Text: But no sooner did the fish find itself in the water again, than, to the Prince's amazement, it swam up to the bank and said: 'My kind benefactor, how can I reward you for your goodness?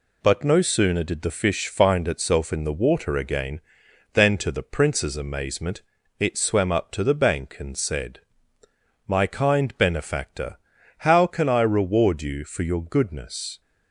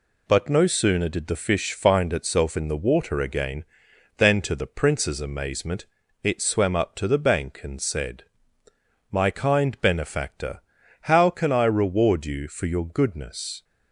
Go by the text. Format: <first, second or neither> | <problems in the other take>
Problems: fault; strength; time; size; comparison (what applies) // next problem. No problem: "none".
neither | none